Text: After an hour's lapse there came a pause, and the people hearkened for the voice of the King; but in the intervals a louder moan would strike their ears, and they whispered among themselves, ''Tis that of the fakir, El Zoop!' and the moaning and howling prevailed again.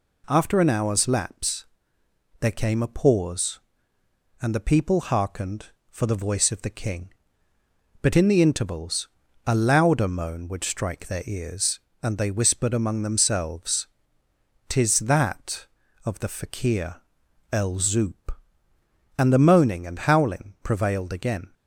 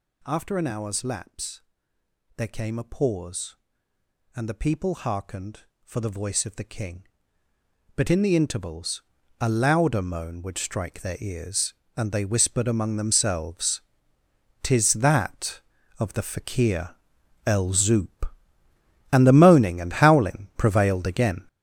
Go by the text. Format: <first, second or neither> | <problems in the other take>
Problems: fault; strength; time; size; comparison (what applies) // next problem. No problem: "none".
first | gets louder; strong; throughout; 9 dB // pauses between "lapse" and "there"; noticeable; at 1.6 s; 0.74 s long; noticeable in the first // pauses between "intervals" and "a"; at 9.0 s; 0.38 s long; also in the first